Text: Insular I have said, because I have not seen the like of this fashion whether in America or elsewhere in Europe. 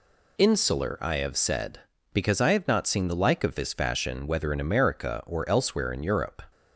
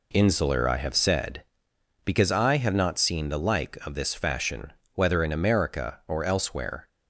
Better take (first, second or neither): first